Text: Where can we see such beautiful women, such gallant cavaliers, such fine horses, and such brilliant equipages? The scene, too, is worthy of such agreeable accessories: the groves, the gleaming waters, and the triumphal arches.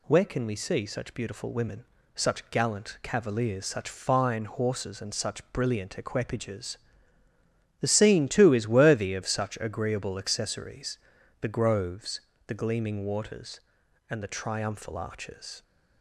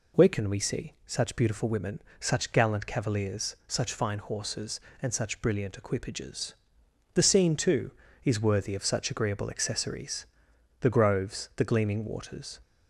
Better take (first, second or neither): first